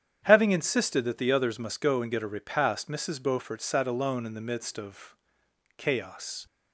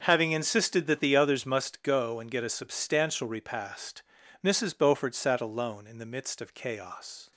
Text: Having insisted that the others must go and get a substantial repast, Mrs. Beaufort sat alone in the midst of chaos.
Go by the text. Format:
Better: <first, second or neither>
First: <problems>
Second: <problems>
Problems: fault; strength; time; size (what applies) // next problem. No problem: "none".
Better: second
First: starts louder than the rest; strong; until 1.2 s; 9 dB // skips "substantial"; at 2.2 s // pauses between "of" and "chaos"; noticeable; at 5.1 s; 0.62 s long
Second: starts louder than the rest; until 1.0 s; 6.5 dB